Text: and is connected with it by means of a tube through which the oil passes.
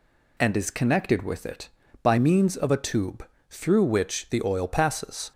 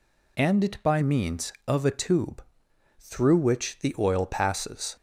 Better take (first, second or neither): first